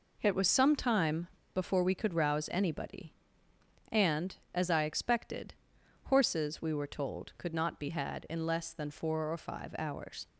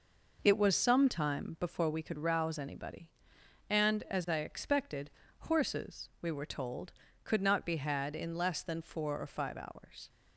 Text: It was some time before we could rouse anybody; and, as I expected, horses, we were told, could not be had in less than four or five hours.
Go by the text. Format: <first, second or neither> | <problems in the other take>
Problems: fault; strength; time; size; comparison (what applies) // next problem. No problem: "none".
second | pauses between "time" and "before"; slight; at 1.2 s; 0.28 s long